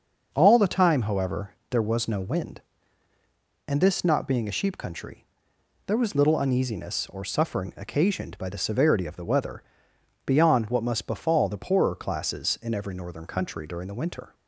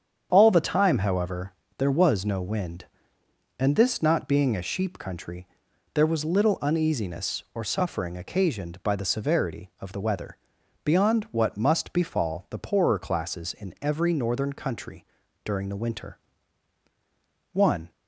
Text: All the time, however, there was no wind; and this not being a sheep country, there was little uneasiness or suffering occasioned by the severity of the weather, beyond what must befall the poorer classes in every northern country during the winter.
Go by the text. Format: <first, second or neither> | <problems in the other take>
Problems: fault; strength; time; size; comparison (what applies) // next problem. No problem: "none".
first | starts louder than the rest; strong; until 1.3 s; 8 dB; also in the first // pauses between "country" and "during"; at 15.0 s; 0.40 s long // goes on to say "One"; slight; from 17.5 s on; 0.40 s long